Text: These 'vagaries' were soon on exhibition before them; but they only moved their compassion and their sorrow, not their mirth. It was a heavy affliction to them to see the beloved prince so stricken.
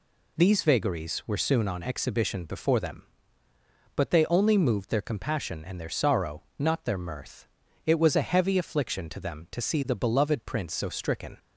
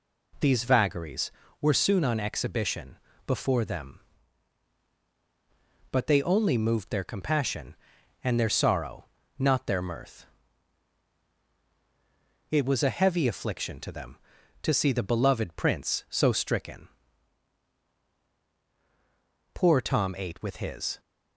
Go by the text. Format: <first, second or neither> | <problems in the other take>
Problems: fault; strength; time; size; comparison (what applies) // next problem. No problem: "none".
first | pauses between "exhibition" and "before"; slight; at 2.9 s; 0.28 s long // goes on to say "Poor Tom ate with his"; from 19.5 s on; 1.4 s long